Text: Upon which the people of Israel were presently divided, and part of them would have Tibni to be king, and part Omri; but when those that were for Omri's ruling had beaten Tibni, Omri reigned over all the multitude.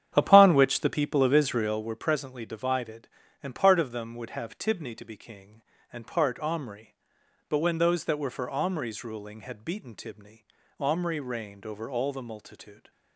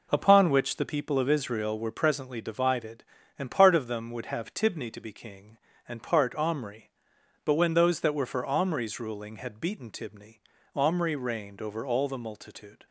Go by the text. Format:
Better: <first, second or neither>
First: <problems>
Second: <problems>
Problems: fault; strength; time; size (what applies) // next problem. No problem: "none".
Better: second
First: starts louder than the rest; strong; until 1.9 s; 9 dB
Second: none